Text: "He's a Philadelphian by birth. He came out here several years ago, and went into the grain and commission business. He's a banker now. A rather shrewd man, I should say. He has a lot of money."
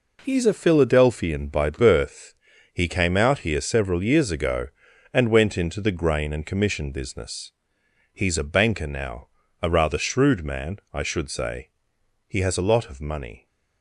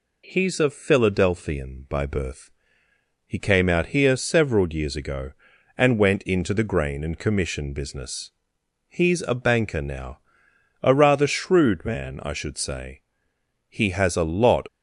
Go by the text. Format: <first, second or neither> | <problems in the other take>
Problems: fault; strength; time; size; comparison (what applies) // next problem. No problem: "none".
first | stops before "of money"; at 14.6 s